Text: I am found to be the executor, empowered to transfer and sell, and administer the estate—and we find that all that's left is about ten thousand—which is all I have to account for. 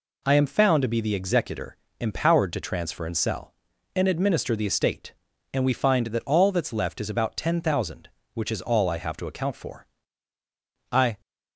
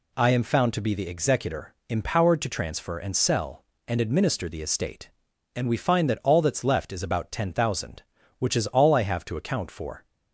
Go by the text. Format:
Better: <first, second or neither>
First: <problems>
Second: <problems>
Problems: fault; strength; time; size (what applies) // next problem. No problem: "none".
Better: second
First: goes on to say "I"; slight; from 10.9 s on; 0.28 s long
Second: none